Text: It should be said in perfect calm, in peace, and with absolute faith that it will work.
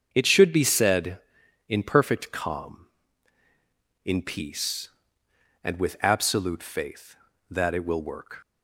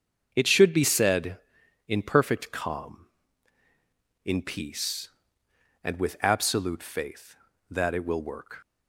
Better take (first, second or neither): neither